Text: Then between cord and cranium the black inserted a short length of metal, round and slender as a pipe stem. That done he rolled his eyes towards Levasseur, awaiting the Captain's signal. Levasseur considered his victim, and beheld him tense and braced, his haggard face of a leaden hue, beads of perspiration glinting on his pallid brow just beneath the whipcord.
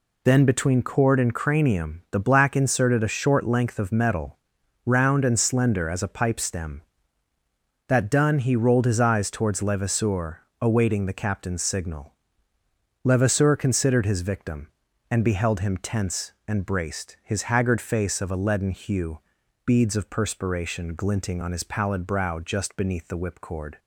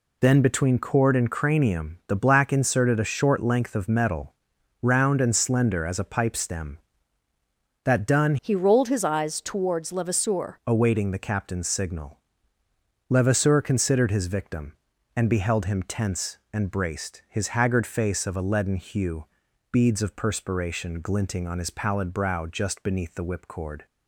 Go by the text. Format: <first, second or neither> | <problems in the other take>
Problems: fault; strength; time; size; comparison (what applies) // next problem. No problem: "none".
first | changes voice from "he" to "Levasseur"; from 8.4 to 10.5 s; 2.1 s long